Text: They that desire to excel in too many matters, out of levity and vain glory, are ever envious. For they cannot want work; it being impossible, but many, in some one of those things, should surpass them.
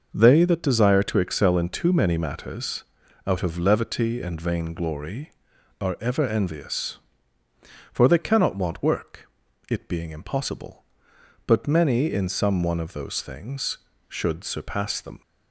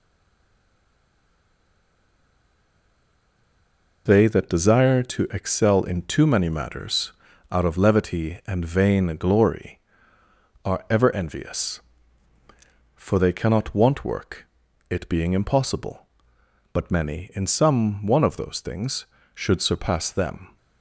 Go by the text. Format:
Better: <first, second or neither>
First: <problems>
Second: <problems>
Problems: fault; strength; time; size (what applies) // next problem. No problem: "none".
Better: first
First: none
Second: stays silent before the first word; strong; until 4.0 s; 4.0 s long